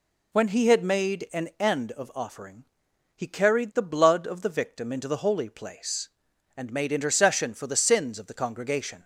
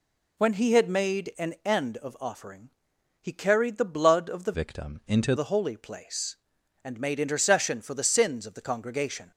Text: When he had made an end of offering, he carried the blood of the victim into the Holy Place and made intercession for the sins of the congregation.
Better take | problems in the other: first | changes voice from "victim" to "into"; from 4.5 to 5.3 s; 0.8 s long

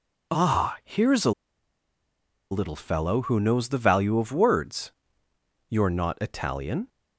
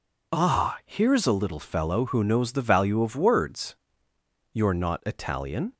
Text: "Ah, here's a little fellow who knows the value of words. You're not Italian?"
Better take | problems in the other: second | pauses between "a" and "little"; at 1.3 s; 1.2 s long

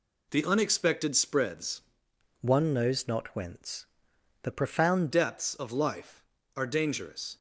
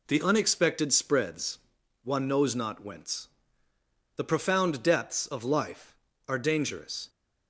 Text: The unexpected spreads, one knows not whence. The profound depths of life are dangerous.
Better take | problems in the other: second | changes voice from "one" to "profound"; from 2.4 to 5.1 s; 2.7 s long

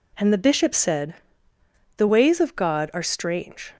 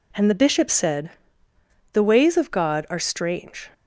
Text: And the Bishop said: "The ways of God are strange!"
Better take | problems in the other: neither | none

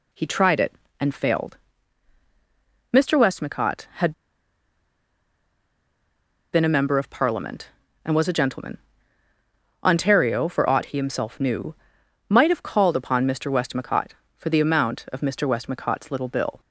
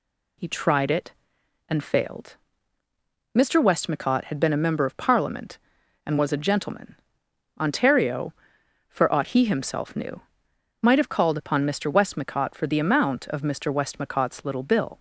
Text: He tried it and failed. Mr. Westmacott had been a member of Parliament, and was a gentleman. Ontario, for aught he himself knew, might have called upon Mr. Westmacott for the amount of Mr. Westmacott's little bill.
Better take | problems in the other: second | pauses between "had" and "been"; strong; at 4.1 s; 2.4 s long

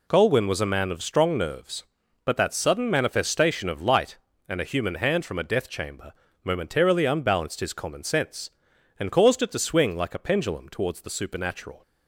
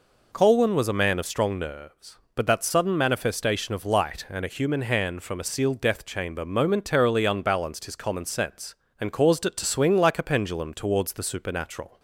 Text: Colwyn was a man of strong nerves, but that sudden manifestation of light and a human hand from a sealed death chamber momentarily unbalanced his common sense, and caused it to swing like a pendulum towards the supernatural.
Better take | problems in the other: second | skips "sealed"; at 5.4 s // pauses between "chamber" and "momentarily"; slight; at 6.1 s; 0.32 s long

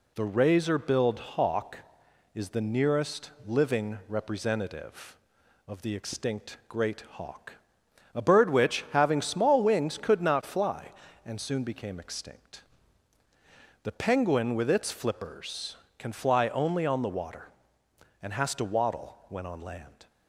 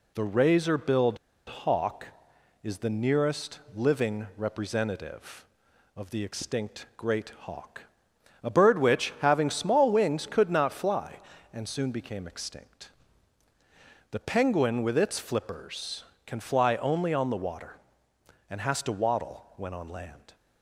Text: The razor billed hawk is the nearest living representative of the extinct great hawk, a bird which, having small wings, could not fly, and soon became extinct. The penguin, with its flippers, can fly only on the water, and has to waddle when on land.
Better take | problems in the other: first | pauses between "billed" and "hawk"; slight; at 1.1 s; 0.30 s long // pauses between "nearest" and "living"; slight; at 3.5 s; 0.16 s long; slight in the first

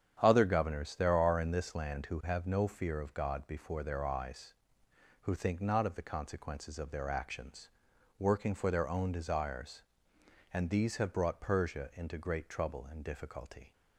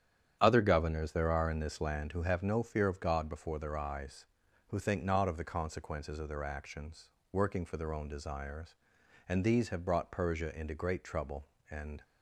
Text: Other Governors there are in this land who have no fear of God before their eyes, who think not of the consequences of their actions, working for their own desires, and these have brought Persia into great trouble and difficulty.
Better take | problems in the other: first | starts louder than the rest; strong; until 1.4 s; 9 dB; strong in the first // stops before "difficulty"; at 12.0 s

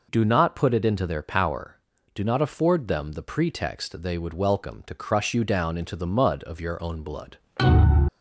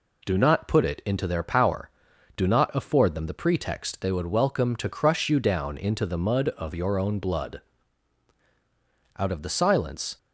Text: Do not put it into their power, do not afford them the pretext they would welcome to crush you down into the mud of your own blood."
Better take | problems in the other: first | goes on to say "Out of the silence"; noticeable; from 9.1 s on; 1.0 s long

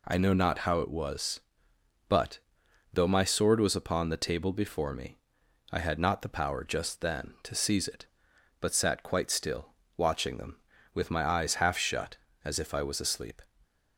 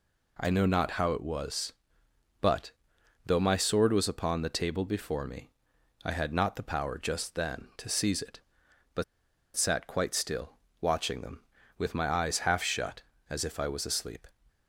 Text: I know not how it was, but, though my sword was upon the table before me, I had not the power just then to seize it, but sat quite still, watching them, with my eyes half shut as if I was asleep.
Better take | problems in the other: first | pauses between "but" and "sat"; noticeable; at 9.0 s; 0.52 s long

